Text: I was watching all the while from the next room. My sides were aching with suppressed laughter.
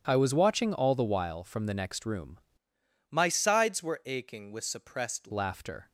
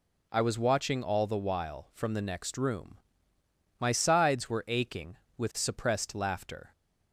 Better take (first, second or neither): second